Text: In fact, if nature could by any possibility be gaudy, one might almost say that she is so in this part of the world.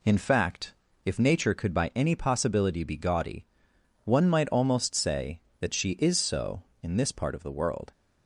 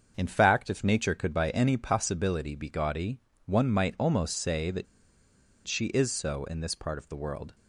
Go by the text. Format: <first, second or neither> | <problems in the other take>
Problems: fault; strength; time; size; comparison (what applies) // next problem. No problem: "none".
first | starts louder than the rest; until 1.1 s; 7 dB // pauses between "that" and "she"; noticeable; at 4.8 s; 0.81 s long